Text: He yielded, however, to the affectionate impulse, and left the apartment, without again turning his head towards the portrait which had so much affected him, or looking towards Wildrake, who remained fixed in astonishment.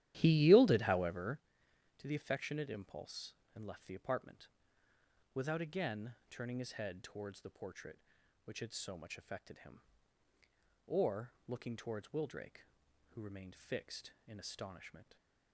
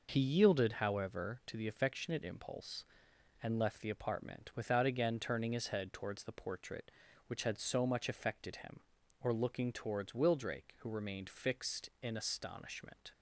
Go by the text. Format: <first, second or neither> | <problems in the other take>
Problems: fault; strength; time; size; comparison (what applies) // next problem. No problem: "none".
second | starts louder than the rest; strong; until 1.4 s; 13 dB // pauses between "again" and "turning"; slight; at 6.1 s; 0.16 s long